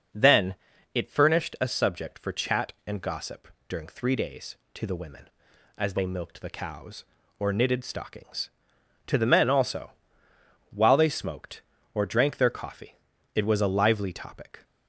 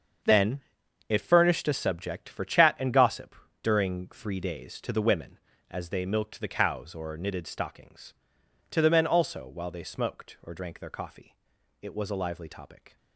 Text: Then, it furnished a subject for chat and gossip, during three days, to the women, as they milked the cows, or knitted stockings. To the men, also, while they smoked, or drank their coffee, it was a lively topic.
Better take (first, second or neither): first